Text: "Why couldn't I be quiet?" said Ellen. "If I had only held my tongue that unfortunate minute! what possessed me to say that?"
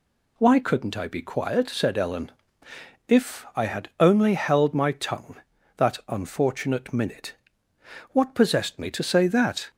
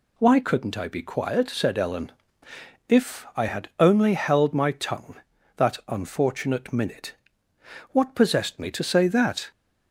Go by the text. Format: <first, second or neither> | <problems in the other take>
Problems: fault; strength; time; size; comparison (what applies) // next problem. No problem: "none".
neither | none